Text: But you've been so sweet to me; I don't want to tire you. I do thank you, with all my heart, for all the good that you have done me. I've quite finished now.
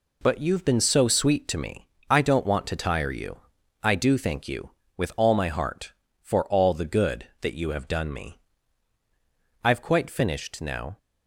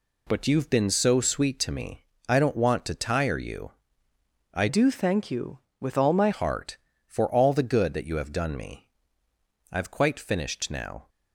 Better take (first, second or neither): first